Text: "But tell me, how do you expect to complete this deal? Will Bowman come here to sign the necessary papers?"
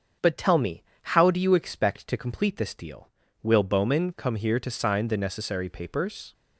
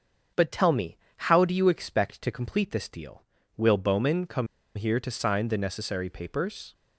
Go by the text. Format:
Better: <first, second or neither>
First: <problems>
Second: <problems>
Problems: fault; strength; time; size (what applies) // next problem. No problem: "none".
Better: first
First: starts louder than the rest; until 1.4 s; 7 dB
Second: starts louder than the rest; until 1.5 s; 7 dB // pauses between "come" and "here"; slight; at 4.4 s; 0.29 s long